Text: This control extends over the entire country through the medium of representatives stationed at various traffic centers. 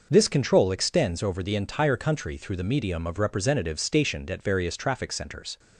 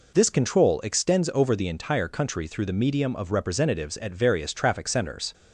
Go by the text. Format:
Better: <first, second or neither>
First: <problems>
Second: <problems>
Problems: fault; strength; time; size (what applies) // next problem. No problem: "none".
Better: first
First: none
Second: skips "stationed"; at 3.9 s